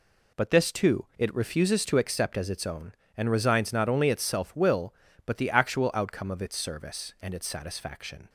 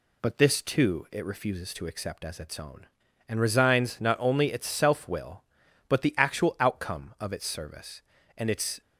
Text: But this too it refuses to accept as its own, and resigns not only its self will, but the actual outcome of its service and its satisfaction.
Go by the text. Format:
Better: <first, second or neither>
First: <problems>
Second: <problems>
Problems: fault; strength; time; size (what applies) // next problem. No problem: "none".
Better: first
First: none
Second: stops before "satisfaction"; at 8.8 s